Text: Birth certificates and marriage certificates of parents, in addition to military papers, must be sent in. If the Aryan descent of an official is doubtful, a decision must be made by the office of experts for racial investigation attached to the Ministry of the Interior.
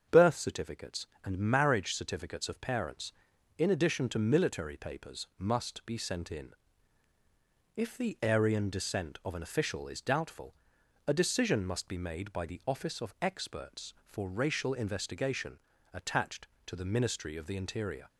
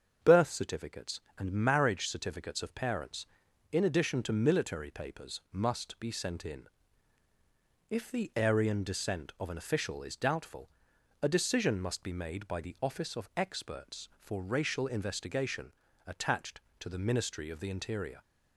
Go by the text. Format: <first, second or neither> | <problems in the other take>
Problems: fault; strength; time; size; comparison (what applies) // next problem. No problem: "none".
neither | starts louder than the rest; the same in both // pauses between "investigation" and "attached"; slight; the same in both